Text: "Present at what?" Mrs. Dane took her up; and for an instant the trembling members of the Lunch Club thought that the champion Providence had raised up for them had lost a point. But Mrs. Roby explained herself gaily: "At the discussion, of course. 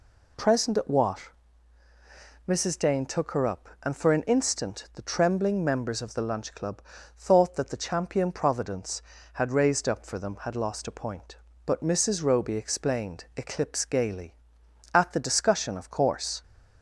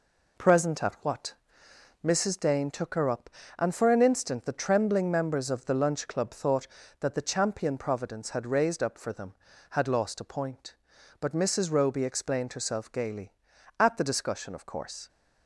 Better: second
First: pauses between "Club" and "thought"; slight; at 6.8 s; 0.34 s long // says "eclipse" for "herself"; at 13.3 s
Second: none

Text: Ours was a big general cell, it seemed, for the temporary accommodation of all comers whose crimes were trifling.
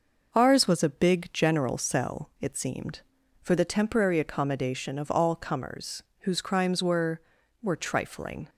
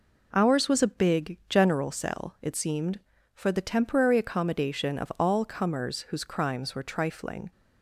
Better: second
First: pauses between "comers" and "whose"; slight; at 6.0 s; 0.16 s long // says "were" twice; at 7.6 s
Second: none

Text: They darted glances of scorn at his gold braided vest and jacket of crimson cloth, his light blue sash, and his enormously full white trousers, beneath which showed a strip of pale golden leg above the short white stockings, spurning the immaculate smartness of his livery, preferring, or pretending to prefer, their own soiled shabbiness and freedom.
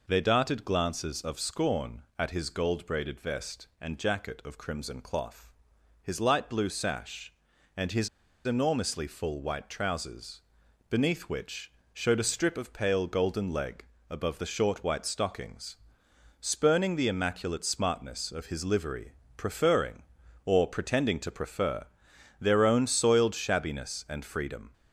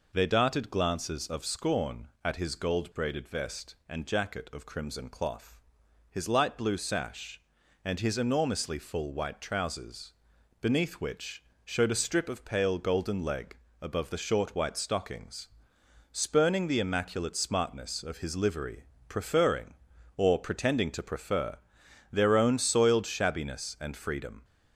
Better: second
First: pauses between "his" and "enormously"; at 8.0 s; 0.36 s long // pauses between "which" and "showed"; slight; at 11.7 s; 0.22 s long // pauses between "leg" and "above"; slight; at 13.8 s; 0.26 s long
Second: pauses between "which" and "showed"; slight; at 11.4 s; 0.22 s long // pauses between "leg" and "above"; slight; at 13.5 s; 0.26 s long

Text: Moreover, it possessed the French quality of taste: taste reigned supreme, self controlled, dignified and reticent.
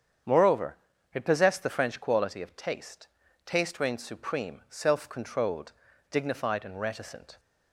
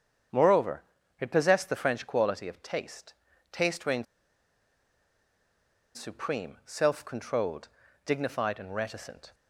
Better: first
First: starts louder than the rest; strong; until 1.6 s; 8 dB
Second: starts louder than the rest; strong; until 1.7 s; 8 dB // pauses between "reigned" and "supreme"; strong; at 4.0 s; 1.9 s long

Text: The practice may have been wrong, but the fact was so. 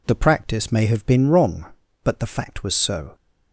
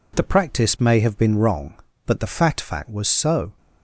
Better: first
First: none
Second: says "fact" twice; at 2.6 s

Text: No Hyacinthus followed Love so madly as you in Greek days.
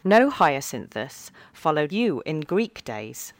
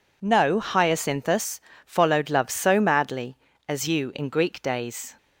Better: second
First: pauses between "Hyacinthus" and "followed"; slight; at 1.3 s; 0.22 s long // skips "Love so madly as"; at 1.9 s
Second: pauses between "Hyacinthus" and "followed"; slight; at 1.5 s; 0.24 s long

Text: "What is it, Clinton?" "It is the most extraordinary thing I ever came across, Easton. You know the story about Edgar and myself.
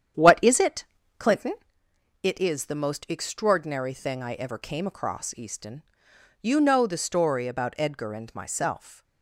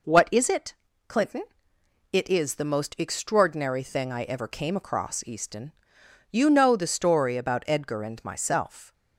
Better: second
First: starts louder than the rest; strong; until 1.8 s; 9 dB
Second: none

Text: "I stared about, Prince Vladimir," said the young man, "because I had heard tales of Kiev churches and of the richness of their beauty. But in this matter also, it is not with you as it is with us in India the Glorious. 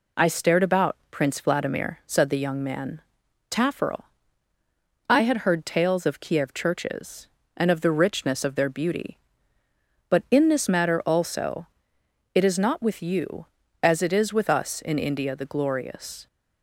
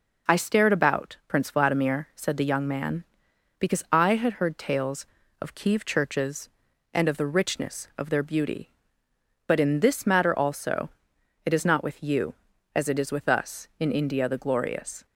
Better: second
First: says "tafferel" for "because"; at 3.4 s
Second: none

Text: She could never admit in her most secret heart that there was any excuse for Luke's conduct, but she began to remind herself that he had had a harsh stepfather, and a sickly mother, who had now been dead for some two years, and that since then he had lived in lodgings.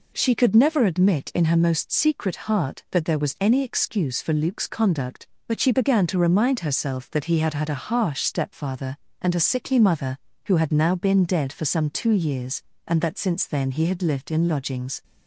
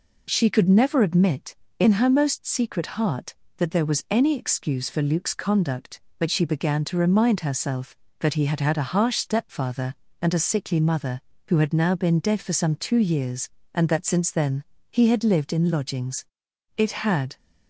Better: first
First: none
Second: pauses between "then" and "he"; slight; at 14.6 s; 0.26 s long // goes on to say "It had"; from 16.7 s on; 0.60 s long

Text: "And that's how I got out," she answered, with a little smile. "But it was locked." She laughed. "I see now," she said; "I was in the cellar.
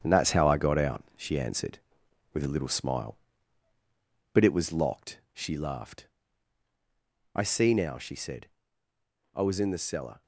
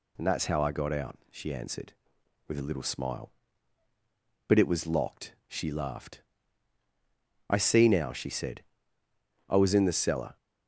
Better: second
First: gets quieter; throughout; 6.5 dB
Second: none

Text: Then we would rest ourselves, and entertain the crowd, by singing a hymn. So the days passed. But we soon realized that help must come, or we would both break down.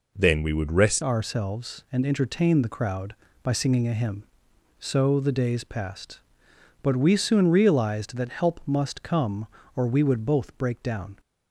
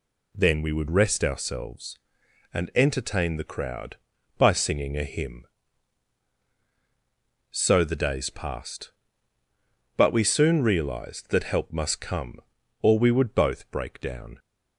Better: second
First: changes voice at "ourselves"; from 1.0 s on; 10.1 s long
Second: none

